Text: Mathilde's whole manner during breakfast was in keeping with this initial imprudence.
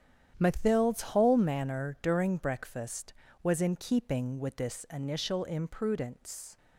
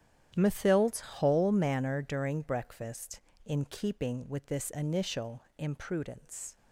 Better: first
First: starts louder than the rest; strong; until 1.3 s; 9.5 dB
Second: starts louder than the rest; strong; until 1.3 s; 10 dB // skips "was"; at 3.3 s // pauses between "initial" and "imprudence"; slight; at 5.4 s; 0.16 s long

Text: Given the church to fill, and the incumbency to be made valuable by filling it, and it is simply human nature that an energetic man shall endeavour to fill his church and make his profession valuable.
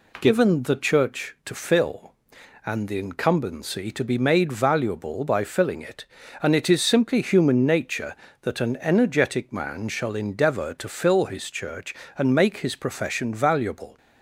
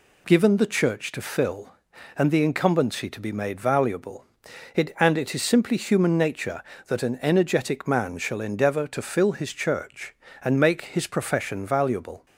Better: first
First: none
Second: skips "by filling"; at 4.4 s

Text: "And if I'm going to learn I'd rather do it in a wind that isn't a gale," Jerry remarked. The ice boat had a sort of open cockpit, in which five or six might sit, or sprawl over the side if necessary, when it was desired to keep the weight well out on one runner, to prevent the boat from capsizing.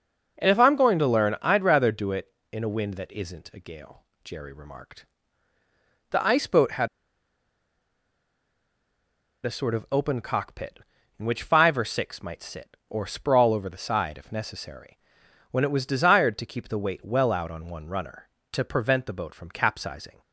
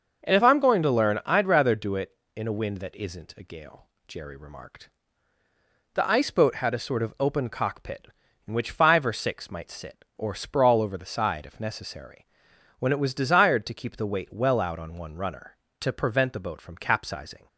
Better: second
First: starts louder than the rest; noticeable; until 1.4 s; 6 dB // pauses between "had" and "a"; strong; at 6.8 s; 2.5 s long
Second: starts louder than the rest; noticeable; until 1.3 s; 6 dB

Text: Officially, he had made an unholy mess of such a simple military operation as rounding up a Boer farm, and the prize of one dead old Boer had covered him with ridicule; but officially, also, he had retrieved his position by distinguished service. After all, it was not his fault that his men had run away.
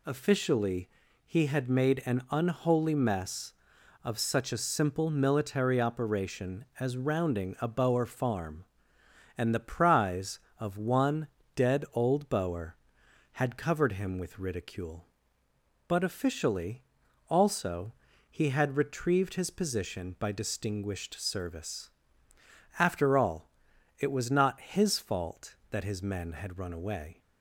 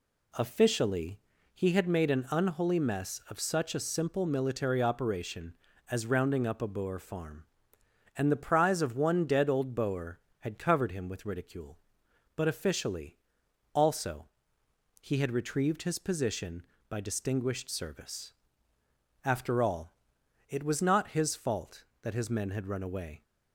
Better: second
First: skips "up"; at 7.5 s // pauses between "one" and "dead"; slight; at 11.2 s; 0.28 s long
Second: none

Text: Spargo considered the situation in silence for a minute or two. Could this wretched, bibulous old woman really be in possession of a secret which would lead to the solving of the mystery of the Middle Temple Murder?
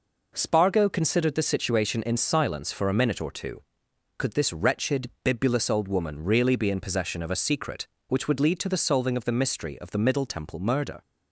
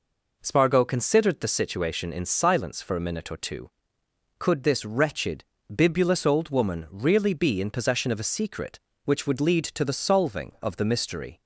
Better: first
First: none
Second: stops before "of the Middle Temple Murder"; at 11.4 s

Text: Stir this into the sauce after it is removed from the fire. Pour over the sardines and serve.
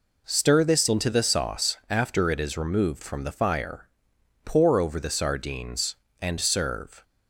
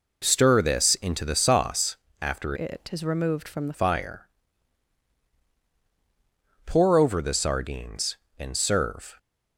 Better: first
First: none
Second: pauses between "sauce" and "after"; slight; at 1.9 s; 0.24 s long // changes voice from "it" to "the"; from 2.5 to 3.7 s; 1.2 s long

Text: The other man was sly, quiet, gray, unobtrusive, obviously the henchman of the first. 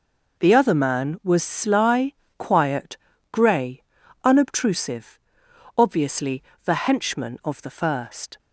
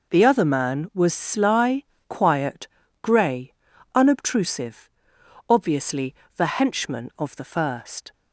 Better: neither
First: pauses between "obviously" and "the"; slight; at 6.4 s; 0.22 s long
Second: pauses between "obviously" and "the"; slight; at 6.1 s; 0.22 s long

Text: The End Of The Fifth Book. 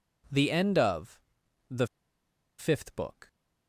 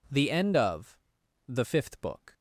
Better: second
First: pauses between "Of" and "The"; noticeable; at 1.2 s; 0.48 s long // pauses between "The" and "Fifth"; noticeable; at 1.8 s; 0.73 s long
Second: pauses between "Of" and "The"; noticeable; at 0.9 s; 0.48 s long

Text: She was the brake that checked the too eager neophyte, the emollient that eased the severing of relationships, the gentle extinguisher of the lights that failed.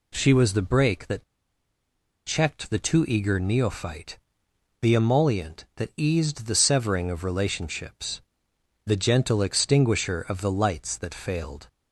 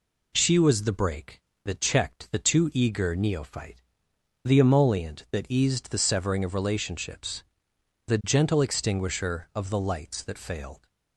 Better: second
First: pauses between "that" and "checked"; at 1.2 s; 1.0 s long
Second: none

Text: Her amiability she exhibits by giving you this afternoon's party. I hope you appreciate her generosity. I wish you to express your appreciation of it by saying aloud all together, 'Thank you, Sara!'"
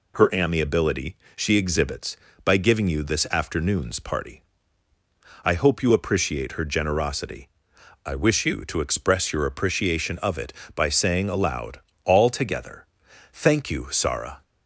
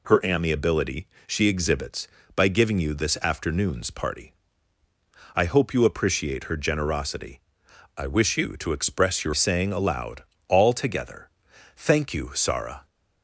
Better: first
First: pauses between "amiability" and "she"; slight; at 1.1 s; 0.18 s long // pauses between "aloud" and "all"; slight; at 11.8 s; 0.24 s long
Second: pauses between "amiability" and "she"; slight; at 1.0 s; 0.18 s long // skips "appreciation of it by"; at 9.3 s // pauses between "aloud" and "all"; slight; at 10.2 s; 0.24 s long

